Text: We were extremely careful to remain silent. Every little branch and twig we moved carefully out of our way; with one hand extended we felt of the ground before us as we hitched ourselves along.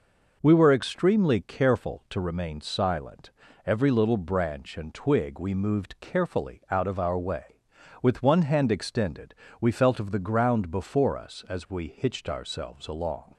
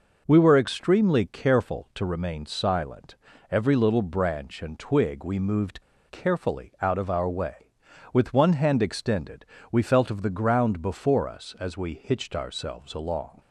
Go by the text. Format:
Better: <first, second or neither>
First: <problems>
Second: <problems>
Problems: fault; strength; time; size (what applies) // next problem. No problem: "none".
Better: first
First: pauses between "extended" and "we"; slight; at 9.3 s; 0.24 s long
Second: pauses between "moved" and "carefully"; slight; at 5.8 s; 0.27 s long // pauses between "extended" and "we"; slight; at 9.4 s; 0.24 s long